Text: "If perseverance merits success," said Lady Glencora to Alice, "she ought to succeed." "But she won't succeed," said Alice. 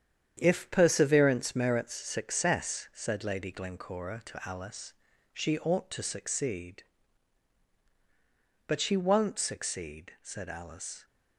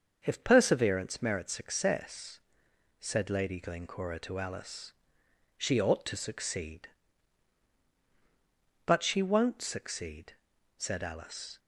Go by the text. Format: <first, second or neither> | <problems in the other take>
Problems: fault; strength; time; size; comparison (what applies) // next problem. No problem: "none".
second | gets quieter; strong; throughout; 7.5 dB // starts louder than the rest; strong; until 1.4 s; 8.5 dB; also in the second